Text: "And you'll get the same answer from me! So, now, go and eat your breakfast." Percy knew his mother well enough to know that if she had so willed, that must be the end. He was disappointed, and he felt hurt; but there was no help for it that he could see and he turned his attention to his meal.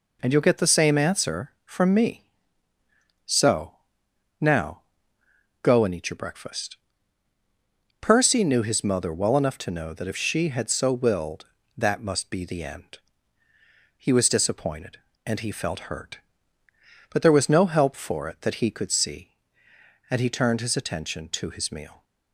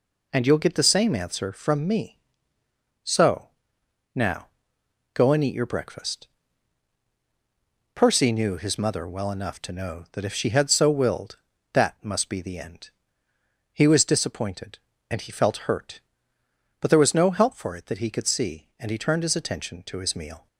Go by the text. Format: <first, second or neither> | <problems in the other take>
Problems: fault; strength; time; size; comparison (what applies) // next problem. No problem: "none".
neither | none